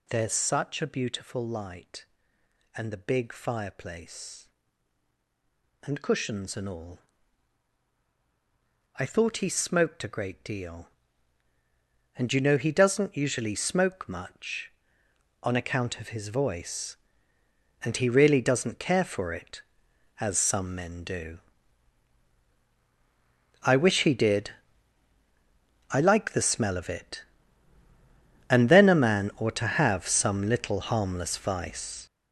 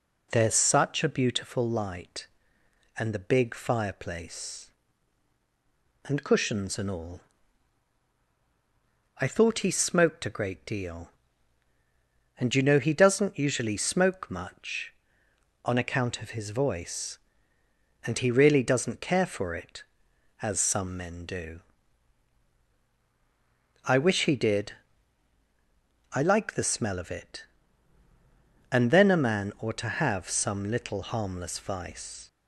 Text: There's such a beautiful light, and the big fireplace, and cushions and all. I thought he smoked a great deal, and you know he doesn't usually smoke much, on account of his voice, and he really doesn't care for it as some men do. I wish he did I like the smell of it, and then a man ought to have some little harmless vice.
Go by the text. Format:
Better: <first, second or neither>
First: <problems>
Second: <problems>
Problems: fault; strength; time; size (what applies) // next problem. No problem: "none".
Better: second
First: gets louder; strong; throughout; 10 dB // pauses between "did" and "I"; strong; at 24.5 s; 1.4 s long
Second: pauses between "did" and "I"; strong; at 24.7 s; 1.4 s long